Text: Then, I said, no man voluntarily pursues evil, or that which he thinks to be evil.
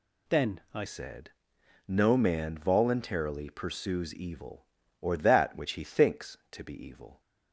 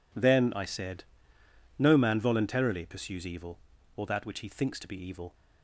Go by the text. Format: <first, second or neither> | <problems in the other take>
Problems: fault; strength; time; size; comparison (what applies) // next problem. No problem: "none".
second | changes voice at "said"; from 0.8 s on; 6.4 s long